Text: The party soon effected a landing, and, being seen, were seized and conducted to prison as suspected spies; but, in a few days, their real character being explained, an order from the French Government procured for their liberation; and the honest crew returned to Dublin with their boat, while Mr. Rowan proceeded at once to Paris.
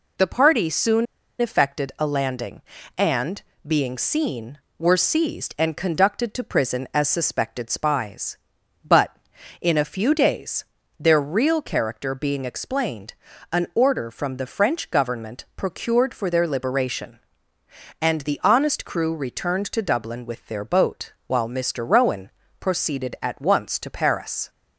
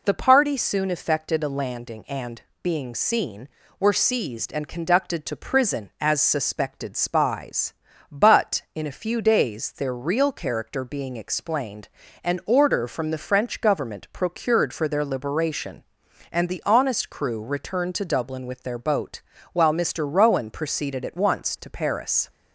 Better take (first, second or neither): second